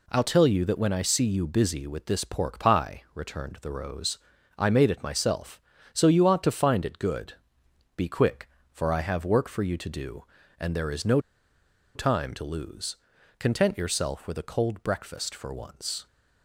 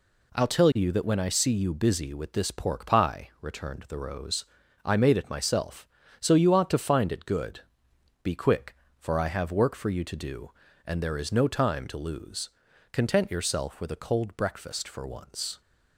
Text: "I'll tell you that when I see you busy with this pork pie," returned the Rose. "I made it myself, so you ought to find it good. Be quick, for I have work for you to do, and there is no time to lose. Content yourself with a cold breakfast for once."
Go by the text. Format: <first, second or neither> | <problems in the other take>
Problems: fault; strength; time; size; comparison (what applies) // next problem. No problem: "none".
second | pauses between "no" and "time"; noticeable; at 11.1 s; 0.76 s long